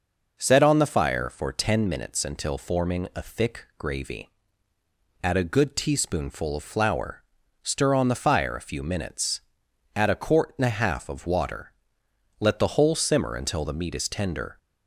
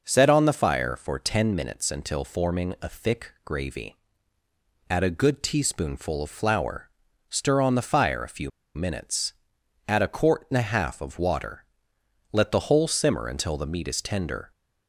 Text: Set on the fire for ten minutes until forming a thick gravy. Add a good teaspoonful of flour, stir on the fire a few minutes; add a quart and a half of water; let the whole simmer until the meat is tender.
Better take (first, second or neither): first